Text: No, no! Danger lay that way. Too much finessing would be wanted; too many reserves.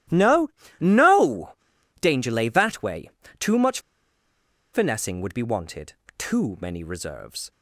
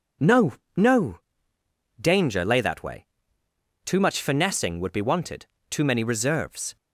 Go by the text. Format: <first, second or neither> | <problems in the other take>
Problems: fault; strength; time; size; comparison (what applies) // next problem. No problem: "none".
second | starts louder than the rest; strong; until 1.4 s; 14.5 dB // pauses between "much" and "finessing"; noticeable; at 3.7 s; 0.94 s long